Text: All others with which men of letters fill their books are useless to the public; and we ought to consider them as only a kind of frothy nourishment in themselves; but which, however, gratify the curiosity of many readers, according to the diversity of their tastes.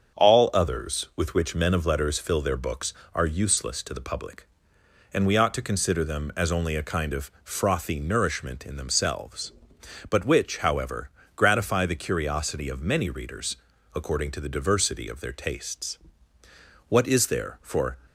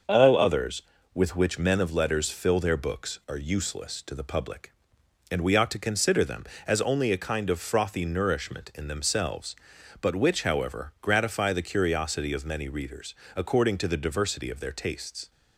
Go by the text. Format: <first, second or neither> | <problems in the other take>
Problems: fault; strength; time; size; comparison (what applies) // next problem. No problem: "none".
second | starts louder than the rest; until 1.2 s; 7 dB; also in the second // goes on to say "What is there for"; noticeable; from 16.8 s on; 1.0 s long